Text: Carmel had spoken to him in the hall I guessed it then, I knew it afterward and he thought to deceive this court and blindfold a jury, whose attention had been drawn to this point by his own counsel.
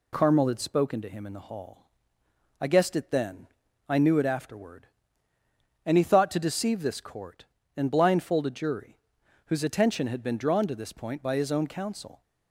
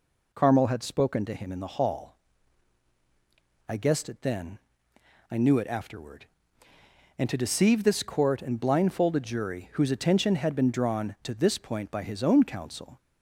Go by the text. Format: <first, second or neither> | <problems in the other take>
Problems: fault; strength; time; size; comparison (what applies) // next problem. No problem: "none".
first | pauses between "hall" and "I"; strong; at 2.1 s; 1.5 s long; noticeable in the first // skips "he thought"; at 7.2 s